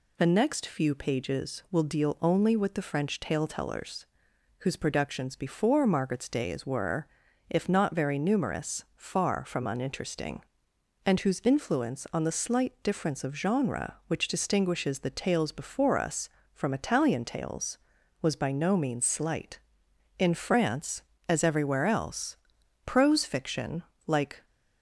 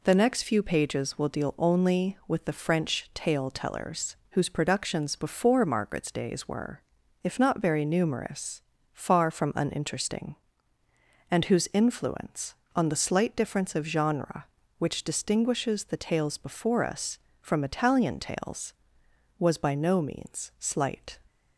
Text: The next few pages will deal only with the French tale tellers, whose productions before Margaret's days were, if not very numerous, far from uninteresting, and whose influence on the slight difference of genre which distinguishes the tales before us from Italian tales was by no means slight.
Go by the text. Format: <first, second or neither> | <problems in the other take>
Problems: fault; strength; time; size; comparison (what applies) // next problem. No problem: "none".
second | goes on to say "In France as everywhere else prose fiction like"; strong; from 20.1 s on; 4.2 s long